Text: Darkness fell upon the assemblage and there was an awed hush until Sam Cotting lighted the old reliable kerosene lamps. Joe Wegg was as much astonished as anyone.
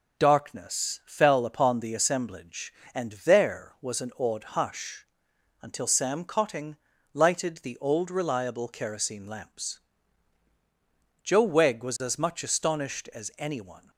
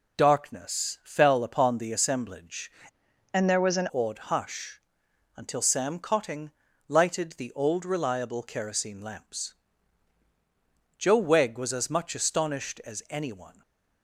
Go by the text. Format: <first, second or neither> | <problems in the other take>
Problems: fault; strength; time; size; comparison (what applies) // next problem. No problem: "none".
first | changes voice from "and" to "an"; from 3.3 to 3.8 s; 0.5 s long // pauses between "hush" and "until"; noticeable; at 4.7 s; 0.56 s long; noticeable in the first // pauses between "Cotting" and "lighted"; at 6.4 s; 0.38 s long; also in the first // stays silent after the last word; slight; from 13.5 s on; 0.5 s long